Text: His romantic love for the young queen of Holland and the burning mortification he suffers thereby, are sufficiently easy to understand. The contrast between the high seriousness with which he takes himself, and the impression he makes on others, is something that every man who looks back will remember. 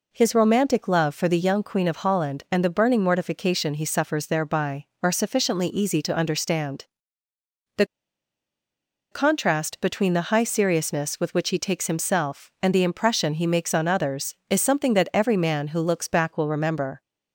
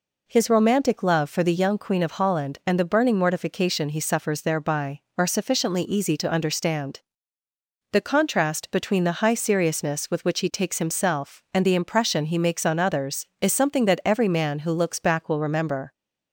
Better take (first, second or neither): second